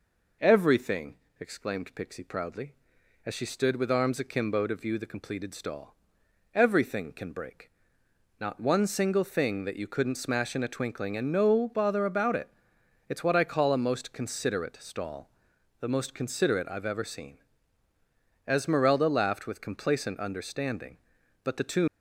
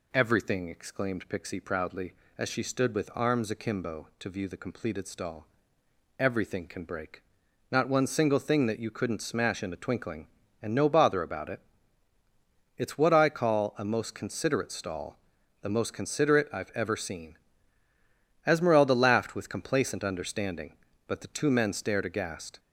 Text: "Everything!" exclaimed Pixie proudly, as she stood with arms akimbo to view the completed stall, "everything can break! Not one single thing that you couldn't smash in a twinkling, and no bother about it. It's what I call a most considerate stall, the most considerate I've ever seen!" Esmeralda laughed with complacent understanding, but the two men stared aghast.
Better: second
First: stops before "men stared aghast"; at 21.8 s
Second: none

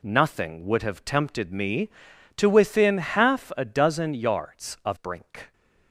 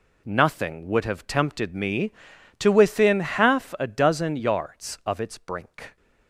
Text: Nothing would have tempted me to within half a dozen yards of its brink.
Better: second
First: skips "its"; at 4.9 s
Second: none

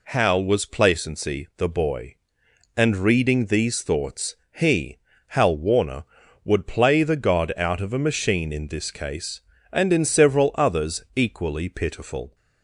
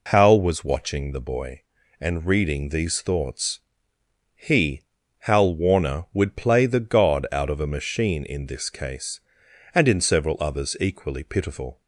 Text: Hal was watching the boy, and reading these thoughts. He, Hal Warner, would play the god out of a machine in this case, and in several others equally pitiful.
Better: second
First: says "placency" for "watching"; at 0.6 s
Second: none

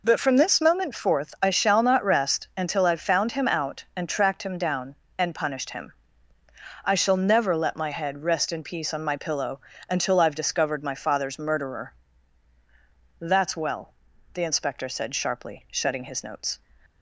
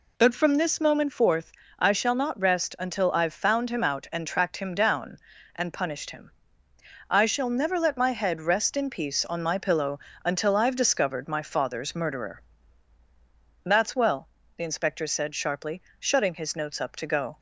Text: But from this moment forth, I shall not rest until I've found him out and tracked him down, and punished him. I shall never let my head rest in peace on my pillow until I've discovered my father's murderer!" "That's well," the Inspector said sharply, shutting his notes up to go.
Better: second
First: pauses between "pillow" and "until"; slight; at 9.6 s; 0.28 s long // stops before "up to go"; at 16.8 s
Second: pauses between "pillow" and "until"; slight; at 9.9 s; 0.24 s long

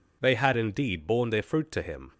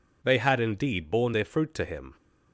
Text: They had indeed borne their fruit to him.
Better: neither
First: none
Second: none

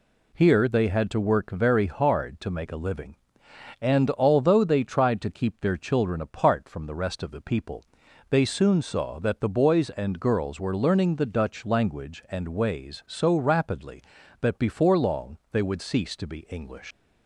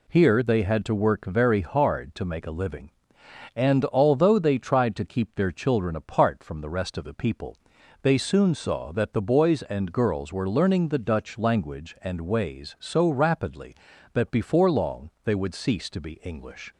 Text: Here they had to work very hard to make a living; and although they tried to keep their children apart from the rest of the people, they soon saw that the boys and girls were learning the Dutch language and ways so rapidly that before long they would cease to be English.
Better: second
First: leaves "English" unfinished; at 16.9 s; 75 ms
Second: none

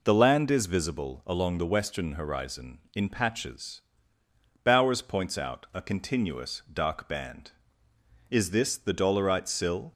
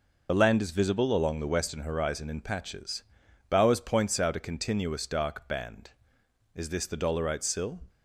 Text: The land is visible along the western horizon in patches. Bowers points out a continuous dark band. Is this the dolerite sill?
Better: first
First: none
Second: loses the start of "The"; at 0.2 s; 40 ms

